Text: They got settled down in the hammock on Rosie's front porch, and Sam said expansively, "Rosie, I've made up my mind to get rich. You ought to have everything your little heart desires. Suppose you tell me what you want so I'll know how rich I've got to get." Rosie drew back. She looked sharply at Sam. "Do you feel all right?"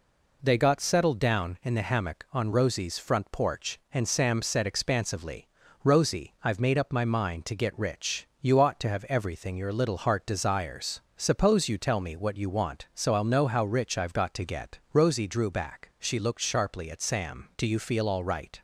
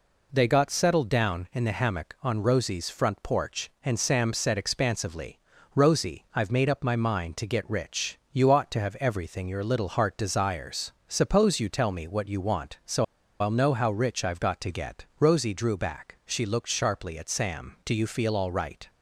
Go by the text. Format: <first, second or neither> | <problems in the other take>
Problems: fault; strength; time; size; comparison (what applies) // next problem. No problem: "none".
first | pauses between "so" and "I'll"; slight; at 13.0 s; 0.35 s long